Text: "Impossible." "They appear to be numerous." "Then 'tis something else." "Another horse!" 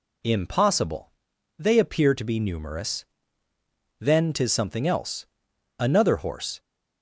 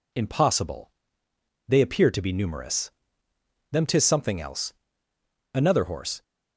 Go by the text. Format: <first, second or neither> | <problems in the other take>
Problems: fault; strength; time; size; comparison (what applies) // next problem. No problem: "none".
first | says "Them" for "Then"; at 3.7 s